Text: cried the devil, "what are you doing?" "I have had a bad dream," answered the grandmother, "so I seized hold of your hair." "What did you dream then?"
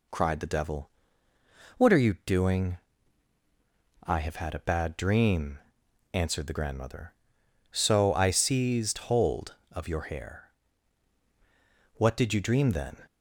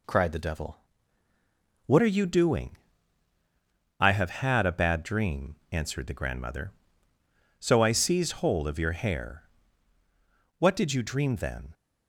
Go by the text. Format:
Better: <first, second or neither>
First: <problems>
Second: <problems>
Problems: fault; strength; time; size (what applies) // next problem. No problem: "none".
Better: first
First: none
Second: changes voice at "are"; from 2.0 s on; 9.7 s long